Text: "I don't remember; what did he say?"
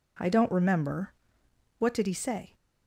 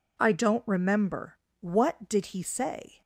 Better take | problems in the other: neither | none

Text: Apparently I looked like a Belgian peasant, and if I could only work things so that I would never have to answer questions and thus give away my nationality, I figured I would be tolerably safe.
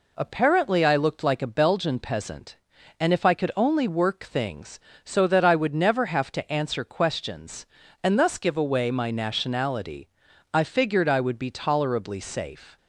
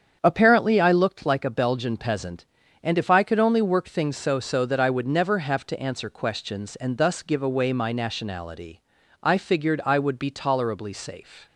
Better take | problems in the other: first | starts louder than the rest; strong; until 1.2 s; 8 dB // says "so" twice; at 4.4 s

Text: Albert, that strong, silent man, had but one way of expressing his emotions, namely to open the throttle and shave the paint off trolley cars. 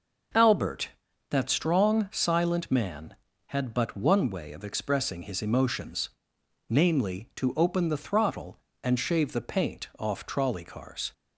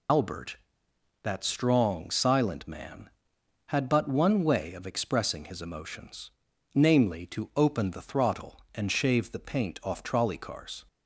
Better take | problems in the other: first | loses the start of "Albert"; at 0.0 s; 95 ms

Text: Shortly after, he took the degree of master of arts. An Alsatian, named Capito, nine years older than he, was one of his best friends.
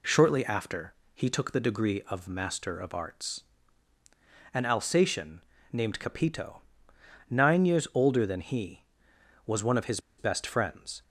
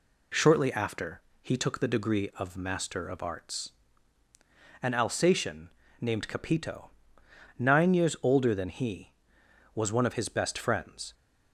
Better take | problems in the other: second | pauses between "his" and "best"; slight; at 9.9 s; 0.19 s long

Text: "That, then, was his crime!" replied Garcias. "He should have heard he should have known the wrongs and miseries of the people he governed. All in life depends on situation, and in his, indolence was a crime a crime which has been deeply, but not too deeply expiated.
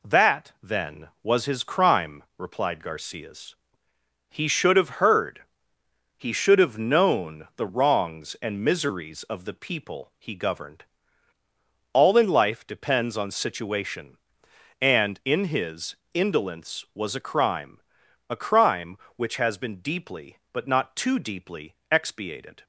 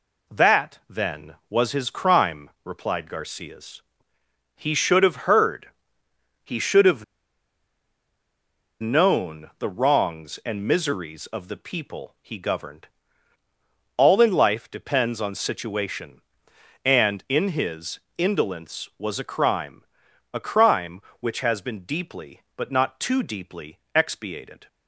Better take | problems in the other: first | pauses between "heard" and "he"; noticeable; at 5.6 s; 0.74 s long; noticeable in the first // pauses between "have" and "known"; strong; at 7.0 s; 1.7 s long // pauses between "crime" and "a"; noticeable; at 19.8 s; 0.48 s long; noticeable in the first // pauses between "deeply" and "expiated"; slight; at 23.7 s; 0.16 s long; slight in the first

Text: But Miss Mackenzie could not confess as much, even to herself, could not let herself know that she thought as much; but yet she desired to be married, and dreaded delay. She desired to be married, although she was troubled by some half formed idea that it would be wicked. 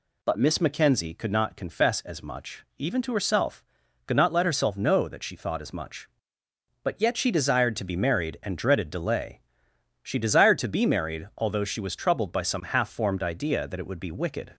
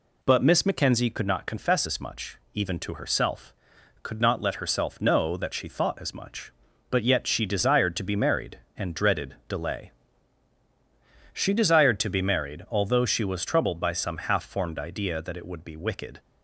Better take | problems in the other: neither | none

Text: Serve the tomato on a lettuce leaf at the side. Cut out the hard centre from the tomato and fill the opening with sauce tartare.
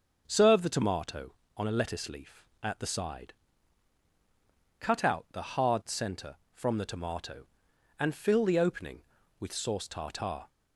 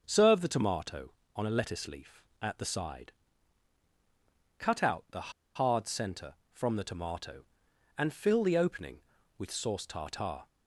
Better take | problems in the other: first | starts louder than the rest; until 1.0 s; 6.5 dB; also in the first // pauses between "the" and "hard"; slight; at 5.3 s; 0.23 s long

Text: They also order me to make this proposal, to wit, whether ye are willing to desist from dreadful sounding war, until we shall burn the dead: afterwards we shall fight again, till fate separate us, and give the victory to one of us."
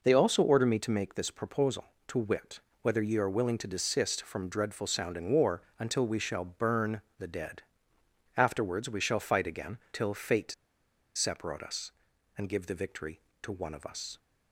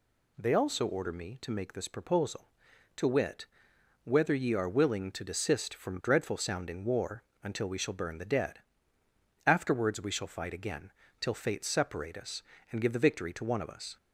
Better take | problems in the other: second | pauses between "burn" and "the"; slight; at 7.0 s; 0.18 s long // pauses between "fate" and "separate"; noticeable; at 10.5 s; 0.62 s long

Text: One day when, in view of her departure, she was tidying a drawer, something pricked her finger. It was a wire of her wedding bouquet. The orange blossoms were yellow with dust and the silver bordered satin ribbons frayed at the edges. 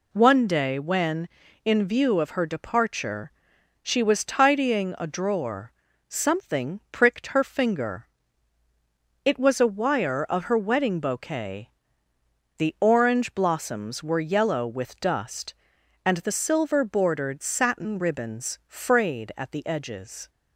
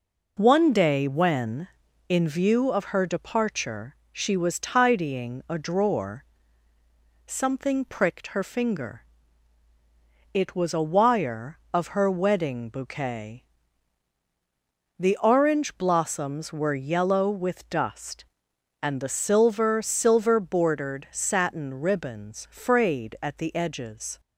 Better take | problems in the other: first | says "silver" twice; at 19.8 s

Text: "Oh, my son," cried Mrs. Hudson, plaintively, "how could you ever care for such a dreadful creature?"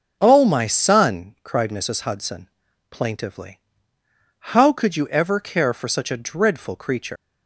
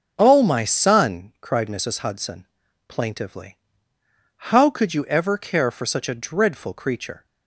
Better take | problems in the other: second | starts louder than the rest; strong; until 1.2 s; 7.5 dB; strong in the second // leaves "creature" unfinished; at 7.1 s; 120 ms

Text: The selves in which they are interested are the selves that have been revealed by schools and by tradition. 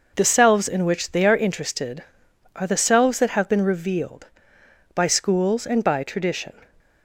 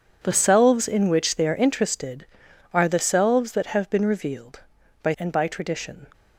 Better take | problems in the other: first | skips "schools"; at 5.1 s

